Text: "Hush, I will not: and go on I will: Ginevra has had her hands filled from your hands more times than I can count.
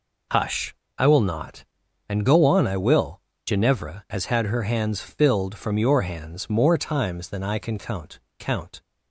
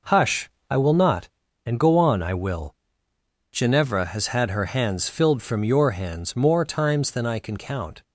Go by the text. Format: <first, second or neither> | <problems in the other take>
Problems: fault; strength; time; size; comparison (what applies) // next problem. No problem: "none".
second | says "count" twice; at 8.4 s